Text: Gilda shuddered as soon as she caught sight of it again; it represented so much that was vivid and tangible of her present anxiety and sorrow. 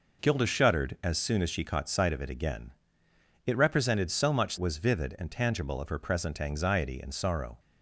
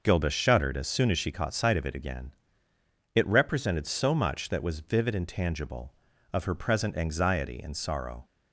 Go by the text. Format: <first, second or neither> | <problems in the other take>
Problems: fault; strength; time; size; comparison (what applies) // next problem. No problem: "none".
second | skips "that"; at 4.5 s